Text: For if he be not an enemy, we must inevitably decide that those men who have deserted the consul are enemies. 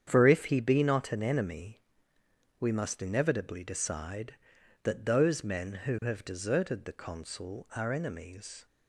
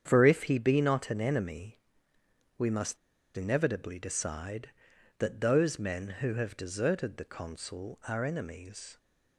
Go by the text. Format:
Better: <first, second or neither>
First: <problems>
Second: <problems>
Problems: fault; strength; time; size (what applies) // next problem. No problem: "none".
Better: first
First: starts louder than the rest; strong; until 1.0 s; 8.5 dB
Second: starts louder than the rest; strong; until 1.0 s; 8.5 dB // pauses between "must" and "inevitably"; at 2.9 s; 0.40 s long